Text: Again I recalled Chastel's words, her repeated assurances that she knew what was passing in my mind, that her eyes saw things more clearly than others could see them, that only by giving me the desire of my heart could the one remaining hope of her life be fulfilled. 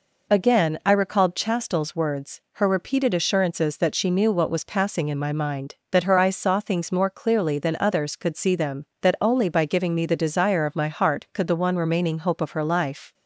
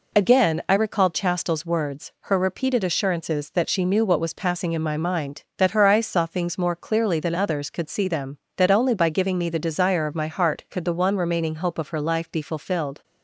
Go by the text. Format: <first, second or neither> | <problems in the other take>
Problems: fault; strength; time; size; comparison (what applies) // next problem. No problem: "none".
second | stops before "be fulfilled"; at 13.1 s